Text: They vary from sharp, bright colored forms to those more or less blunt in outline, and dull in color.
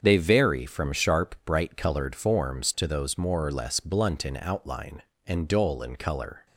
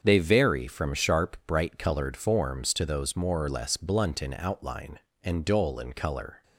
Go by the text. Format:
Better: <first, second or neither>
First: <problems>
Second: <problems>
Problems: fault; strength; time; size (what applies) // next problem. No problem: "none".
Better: neither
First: starts louder than the rest; until 1.0 s; 7 dB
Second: starts louder than the rest; until 1.0 s; 7 dB